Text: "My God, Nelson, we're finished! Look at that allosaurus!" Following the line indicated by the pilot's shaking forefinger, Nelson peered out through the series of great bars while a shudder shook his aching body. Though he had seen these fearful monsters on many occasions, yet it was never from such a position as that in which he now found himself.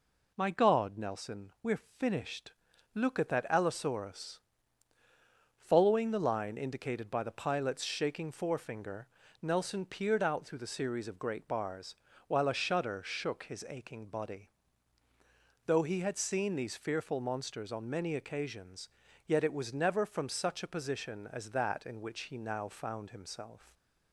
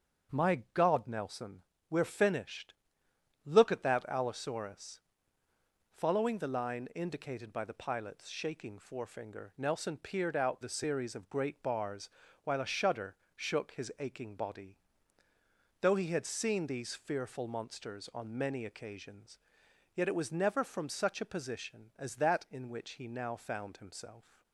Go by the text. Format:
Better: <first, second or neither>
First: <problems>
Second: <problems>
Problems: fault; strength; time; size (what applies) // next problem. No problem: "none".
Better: first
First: pauses between "bars" and "while"; slight; at 11.9 s; 0.32 s long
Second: starts louder than the rest; until 1.4 s; 7 dB // skips "through"; at 10.6 s // pauses between "bars" and "while"; slight; at 12.0 s; 0.36 s long // pauses between "shudder" and "shook"; slight; at 13.1 s; 0.20 s long